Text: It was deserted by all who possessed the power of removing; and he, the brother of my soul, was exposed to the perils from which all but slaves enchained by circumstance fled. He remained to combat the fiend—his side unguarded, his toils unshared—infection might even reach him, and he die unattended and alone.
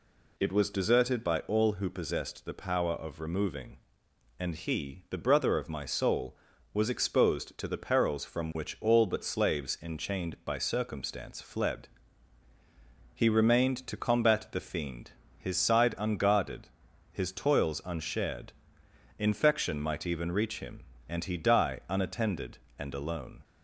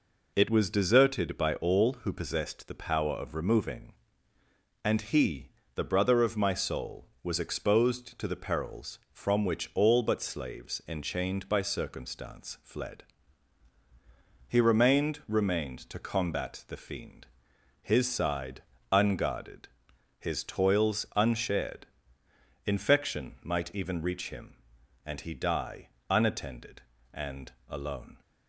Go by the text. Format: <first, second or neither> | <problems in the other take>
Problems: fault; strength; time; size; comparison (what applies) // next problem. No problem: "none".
first | says "remained" twice; at 15.2 s // pauses between "side" and "unguarded"; slight; at 18.6 s; 0.28 s long // pauses between "die" and "unattended"; slight; at 25.8 s; 0.20 s long // pauses between "and" and "alone"; slight; at 27.5 s; 0.16 s long